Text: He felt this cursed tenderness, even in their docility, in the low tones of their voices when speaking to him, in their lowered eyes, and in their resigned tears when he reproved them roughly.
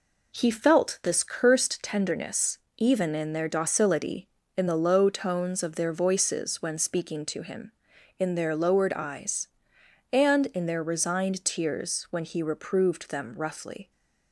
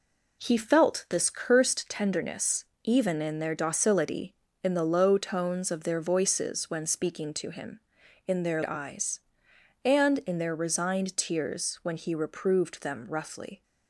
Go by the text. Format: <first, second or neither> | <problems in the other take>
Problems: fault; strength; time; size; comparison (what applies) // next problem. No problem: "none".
first | skips "lowered"; at 8.6 s